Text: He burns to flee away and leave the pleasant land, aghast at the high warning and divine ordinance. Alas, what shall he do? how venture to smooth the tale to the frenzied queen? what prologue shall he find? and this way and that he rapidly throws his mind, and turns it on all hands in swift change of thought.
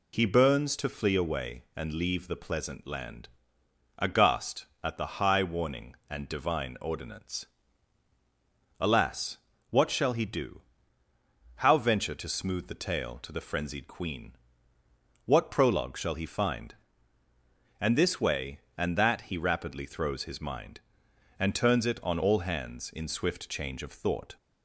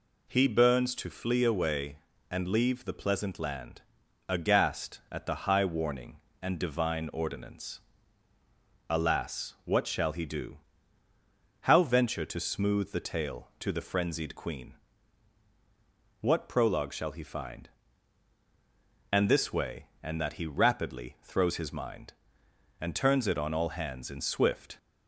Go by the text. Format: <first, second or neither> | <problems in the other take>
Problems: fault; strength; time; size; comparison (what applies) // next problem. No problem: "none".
first | stops before "change of thought"; at 24.7 s